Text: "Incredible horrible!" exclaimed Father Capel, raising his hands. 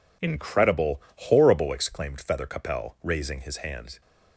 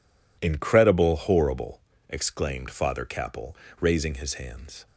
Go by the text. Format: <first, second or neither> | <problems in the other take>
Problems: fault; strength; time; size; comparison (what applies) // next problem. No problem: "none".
second | says "Feather" for "Father"; at 2.2 s